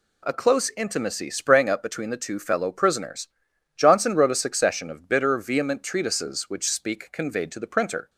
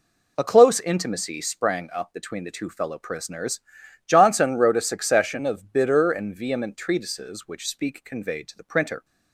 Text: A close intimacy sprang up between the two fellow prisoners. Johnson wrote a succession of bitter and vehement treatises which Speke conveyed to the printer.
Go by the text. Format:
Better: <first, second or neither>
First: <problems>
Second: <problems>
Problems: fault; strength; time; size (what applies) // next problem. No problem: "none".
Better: second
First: skips "and"; at 5.3 s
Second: none